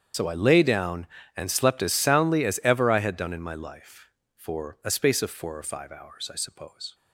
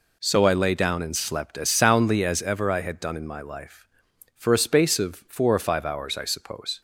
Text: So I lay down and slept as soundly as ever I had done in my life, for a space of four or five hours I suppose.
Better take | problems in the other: second | loses the start of "So"; at 0.1 s; 55 ms // starts louder than the rest; strong; until 1.4 s; 8 dB

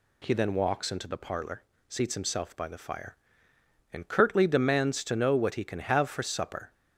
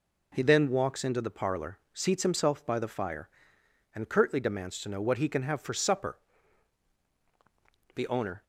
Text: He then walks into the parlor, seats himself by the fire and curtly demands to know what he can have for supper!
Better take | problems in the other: first | goes on to say "The owner"; from 7.9 s on; 0.50 s long

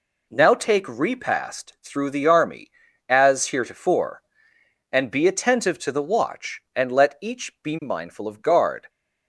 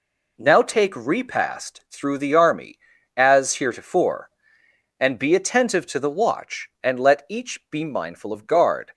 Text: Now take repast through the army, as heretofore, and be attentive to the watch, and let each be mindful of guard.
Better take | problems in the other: neither | none

